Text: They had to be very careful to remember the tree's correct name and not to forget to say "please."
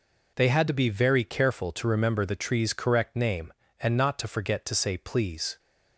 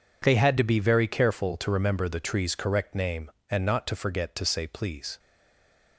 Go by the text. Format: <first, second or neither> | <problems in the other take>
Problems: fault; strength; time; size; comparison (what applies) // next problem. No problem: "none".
first | stays silent after the last word; slight; from 5.1 s on; 0.8 s long